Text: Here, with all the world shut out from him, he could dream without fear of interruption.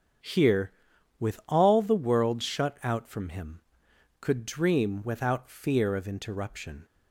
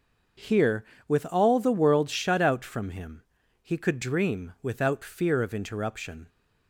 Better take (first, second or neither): second